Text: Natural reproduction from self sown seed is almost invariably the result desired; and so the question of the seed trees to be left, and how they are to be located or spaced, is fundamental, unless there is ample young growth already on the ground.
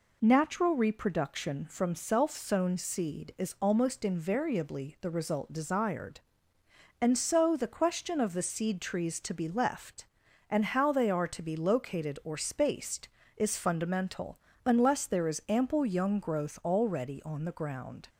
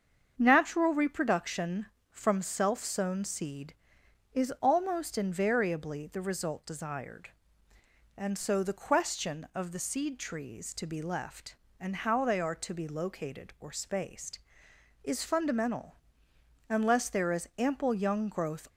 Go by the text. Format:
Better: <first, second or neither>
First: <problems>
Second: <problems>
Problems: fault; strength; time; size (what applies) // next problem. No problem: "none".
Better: first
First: none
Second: starts louder than the rest; until 1.3 s; 7 dB // stops before "already on the ground"; at 18.6 s